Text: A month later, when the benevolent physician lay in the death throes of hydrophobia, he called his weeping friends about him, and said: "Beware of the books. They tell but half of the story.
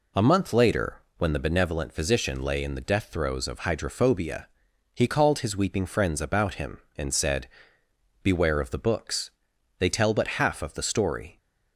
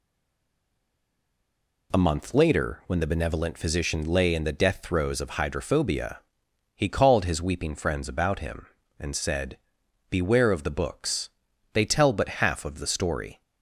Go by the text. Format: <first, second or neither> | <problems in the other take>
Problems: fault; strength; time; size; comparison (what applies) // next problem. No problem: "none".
first | stays silent before the first word; noticeable; until 1.9 s; 1.9 s long